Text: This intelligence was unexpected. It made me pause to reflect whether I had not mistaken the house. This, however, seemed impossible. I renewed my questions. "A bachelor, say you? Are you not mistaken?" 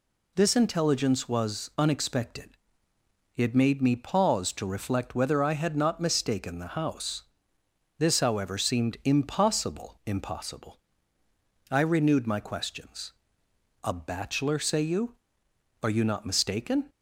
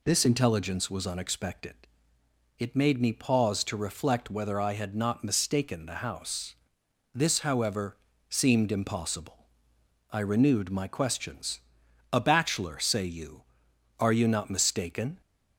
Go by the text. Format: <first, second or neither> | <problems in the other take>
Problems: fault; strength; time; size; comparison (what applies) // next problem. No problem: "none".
second | says "impossible" twice; at 10.0 s